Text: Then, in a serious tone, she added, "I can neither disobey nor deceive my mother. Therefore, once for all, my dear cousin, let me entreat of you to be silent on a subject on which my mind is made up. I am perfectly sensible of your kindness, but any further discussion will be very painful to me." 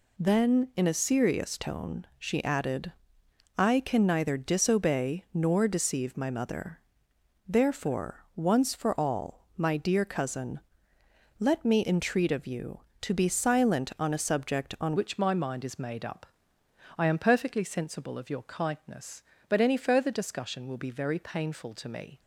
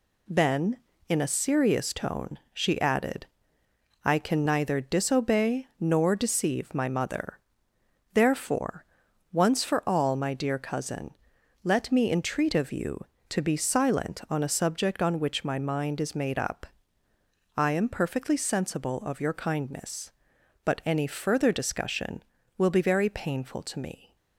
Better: second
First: changes voice at "which"; from 14.9 s on; 7.2 s long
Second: none

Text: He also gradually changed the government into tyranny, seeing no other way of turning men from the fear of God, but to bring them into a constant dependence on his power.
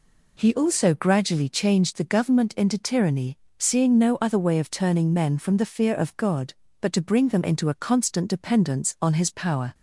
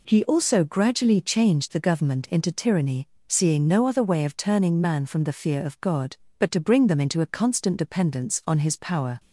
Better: first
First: none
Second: says "man" for "men"; at 4.7 s

